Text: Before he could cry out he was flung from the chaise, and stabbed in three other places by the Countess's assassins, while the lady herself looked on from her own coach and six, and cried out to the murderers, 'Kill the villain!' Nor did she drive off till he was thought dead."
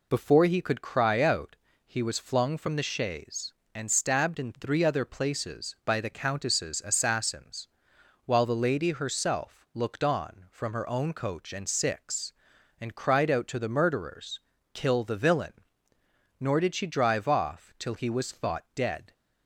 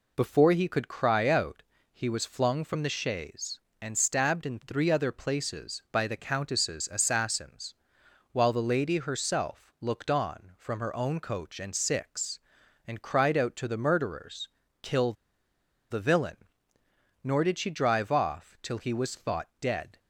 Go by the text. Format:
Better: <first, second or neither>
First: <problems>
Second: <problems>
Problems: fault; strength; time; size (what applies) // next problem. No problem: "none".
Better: first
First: pauses between "out" and "he"; slight; at 1.5 s; 0.30 s long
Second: pauses between "out" and "he"; slight; at 1.6 s; 0.30 s long // pauses between "Kill" and "the"; noticeable; at 15.1 s; 0.77 s long